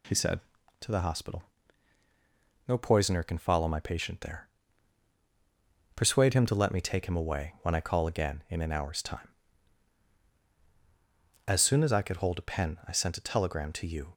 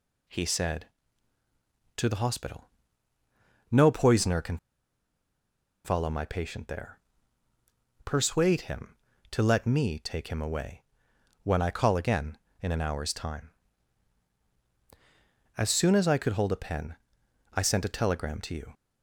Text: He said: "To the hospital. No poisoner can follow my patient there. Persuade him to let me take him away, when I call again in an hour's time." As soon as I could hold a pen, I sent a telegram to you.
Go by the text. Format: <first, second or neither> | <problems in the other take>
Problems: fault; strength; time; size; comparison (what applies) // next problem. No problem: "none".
first | pauses between "can" and "follow"; strong; at 4.5 s; 1.2 s long